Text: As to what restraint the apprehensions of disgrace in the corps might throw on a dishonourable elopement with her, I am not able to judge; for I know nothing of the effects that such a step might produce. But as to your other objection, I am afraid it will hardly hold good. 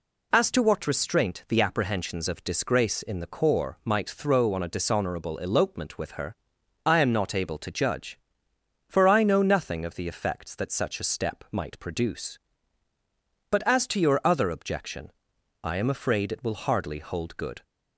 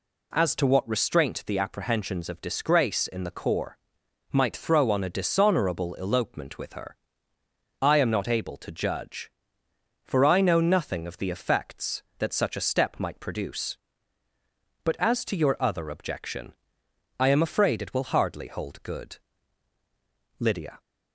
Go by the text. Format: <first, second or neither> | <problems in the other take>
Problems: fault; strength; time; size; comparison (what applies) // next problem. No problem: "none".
first | pauses between "corps" and "might"; noticeable; at 3.7 s; 0.56 s long // goes on to say "Lydia"; slight; from 20.3 s on; 0.40 s long